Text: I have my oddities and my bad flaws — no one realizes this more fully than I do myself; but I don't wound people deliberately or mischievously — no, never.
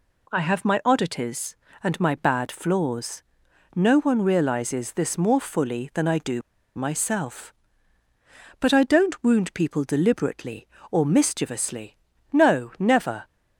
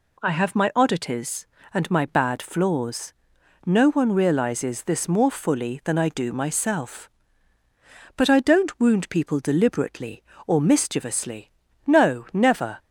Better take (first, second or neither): second